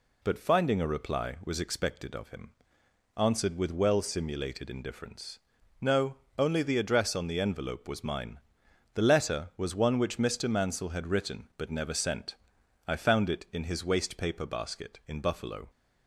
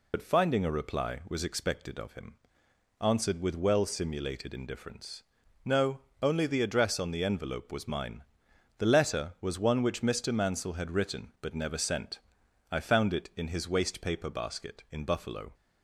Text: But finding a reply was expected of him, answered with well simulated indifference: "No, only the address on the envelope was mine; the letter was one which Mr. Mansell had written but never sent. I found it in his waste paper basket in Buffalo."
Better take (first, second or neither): first